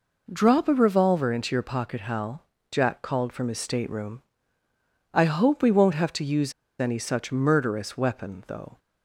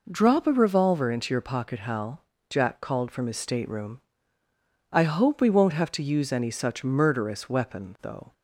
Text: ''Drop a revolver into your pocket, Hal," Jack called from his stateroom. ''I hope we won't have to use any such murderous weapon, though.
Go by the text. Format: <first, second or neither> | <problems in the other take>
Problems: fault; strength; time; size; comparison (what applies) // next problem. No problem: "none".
second | pauses between "use" and "any"; slight; at 6.5 s; 0.28 s long